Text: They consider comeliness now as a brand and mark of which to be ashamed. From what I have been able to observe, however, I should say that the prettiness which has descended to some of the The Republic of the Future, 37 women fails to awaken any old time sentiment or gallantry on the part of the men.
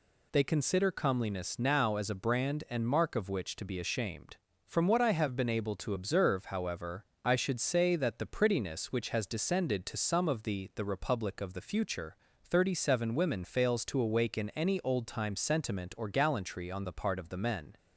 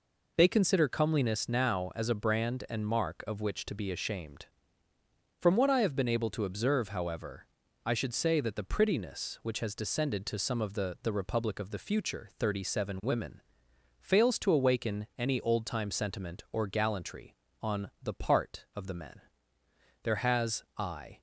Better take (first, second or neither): first